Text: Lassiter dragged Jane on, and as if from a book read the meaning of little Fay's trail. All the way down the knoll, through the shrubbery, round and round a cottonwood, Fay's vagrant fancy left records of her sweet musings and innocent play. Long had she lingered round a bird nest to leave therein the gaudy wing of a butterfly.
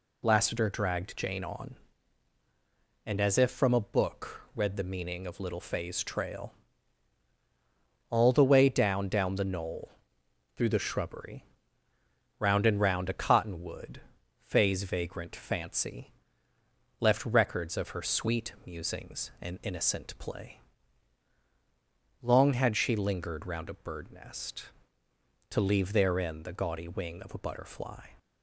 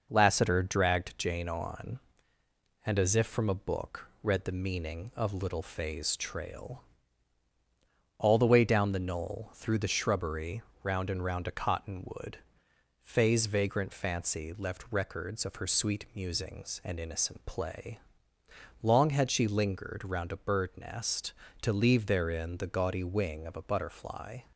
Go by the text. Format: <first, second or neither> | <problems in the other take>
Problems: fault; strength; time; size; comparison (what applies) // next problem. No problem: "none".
second | pauses between "book" and "read"; slight; at 4.3 s; 0.16 s long; slight in the second // says "down" twice; at 9.0 s // pauses between "fancy" and "left"; noticeable; at 16.0 s; 0.90 s long